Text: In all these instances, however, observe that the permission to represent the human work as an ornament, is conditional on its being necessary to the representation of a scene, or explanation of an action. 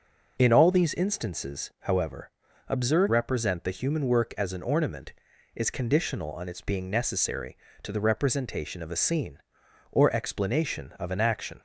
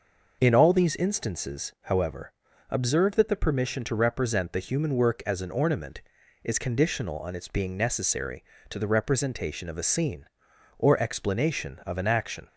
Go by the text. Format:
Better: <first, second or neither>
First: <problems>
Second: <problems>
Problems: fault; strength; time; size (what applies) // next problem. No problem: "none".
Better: second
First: skips "that the permission to"; at 3.0 s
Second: none